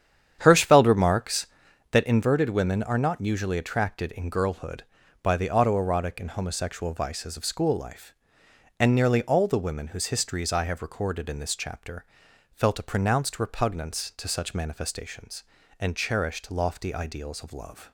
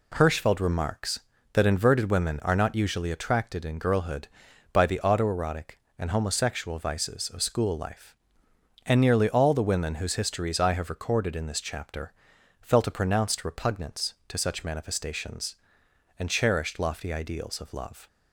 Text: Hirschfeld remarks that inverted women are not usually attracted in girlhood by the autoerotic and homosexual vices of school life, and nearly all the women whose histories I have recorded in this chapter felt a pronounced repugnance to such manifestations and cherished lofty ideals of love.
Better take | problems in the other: second | starts louder than the rest; strong; until 2.0 s; 9 dB // pauses between "chapter" and "felt"; noticeable; at 12.0 s; 0.48 s long; noticeable in the second

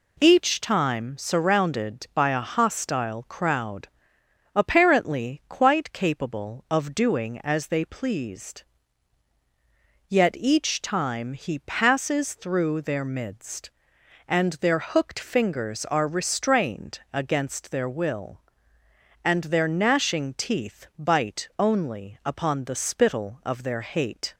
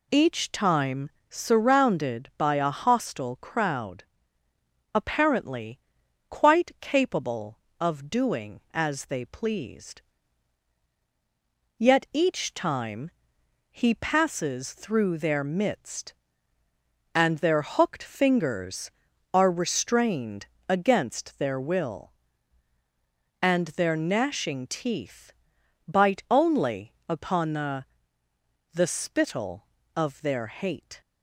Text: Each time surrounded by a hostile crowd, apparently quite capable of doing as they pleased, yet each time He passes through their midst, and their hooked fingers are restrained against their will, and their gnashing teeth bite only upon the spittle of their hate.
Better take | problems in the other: first | pauses between "time" and "surrounded"; slight; at 1.1 s; 0.18 s long // pauses between "apparently" and "quite"; noticeable; at 5.8 s; 0.48 s long // pauses between "time" and "He"; noticeable; at 13.1 s; 0.62 s long // pauses between "restrained" and "against"; slight; at 20.4 s; 0.22 s long // pauses between "teeth" and "bite"; noticeable; at 25.3 s; 0.56 s long // says "the" twice; at 28.7 s

